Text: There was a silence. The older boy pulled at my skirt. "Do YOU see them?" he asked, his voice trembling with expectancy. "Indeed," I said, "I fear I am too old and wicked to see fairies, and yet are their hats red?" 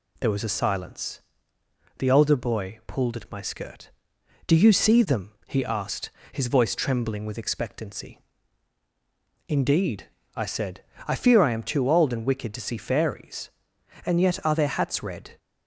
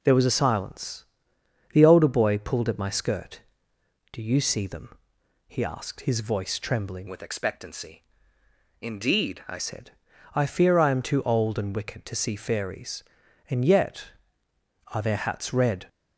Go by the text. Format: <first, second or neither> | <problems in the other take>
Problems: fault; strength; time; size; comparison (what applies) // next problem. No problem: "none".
first | changes voice from "with" to "I"; from 7.0 to 9.5 s; 2.5 s long